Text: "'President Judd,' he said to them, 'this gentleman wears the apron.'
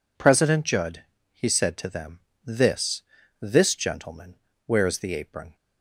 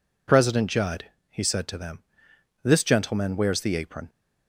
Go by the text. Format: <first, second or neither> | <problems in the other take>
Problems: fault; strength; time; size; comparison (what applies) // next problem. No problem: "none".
second | says "this" twice; at 3.4 s // pauses between "gentleman" and "wears"; slight; at 4.3 s; 0.32 s long